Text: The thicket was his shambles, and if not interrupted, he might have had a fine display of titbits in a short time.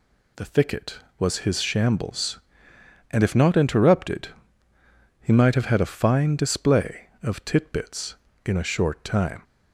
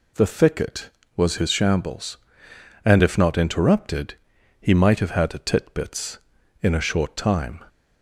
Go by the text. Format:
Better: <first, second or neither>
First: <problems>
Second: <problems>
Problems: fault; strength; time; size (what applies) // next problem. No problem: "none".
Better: first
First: none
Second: skips "fine display of"; at 5.3 s